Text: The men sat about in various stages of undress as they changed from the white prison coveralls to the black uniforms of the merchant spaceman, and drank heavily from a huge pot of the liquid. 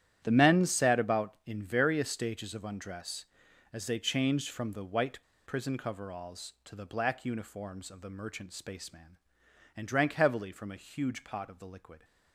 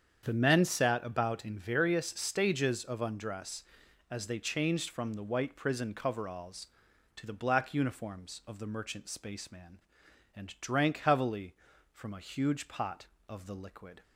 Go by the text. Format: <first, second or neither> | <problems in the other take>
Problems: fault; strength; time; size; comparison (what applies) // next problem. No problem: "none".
second | starts louder than the rest; strong; until 1.2 s; 11 dB; strong in the second // pauses between "white" and "prison"; slight; at 5.1 s; 0.28 s long